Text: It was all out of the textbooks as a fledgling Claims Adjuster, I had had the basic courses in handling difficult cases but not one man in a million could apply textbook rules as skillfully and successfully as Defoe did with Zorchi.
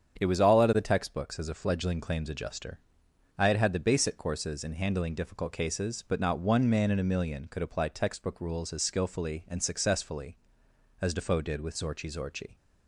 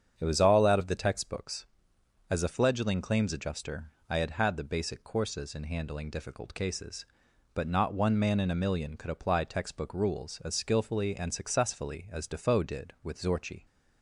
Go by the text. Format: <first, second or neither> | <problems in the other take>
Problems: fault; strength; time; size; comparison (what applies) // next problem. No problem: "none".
second | starts louder than the rest; strong; until 1.2 s; 8 dB; strong in the second // says "Zorchi" twice; at 12.1 s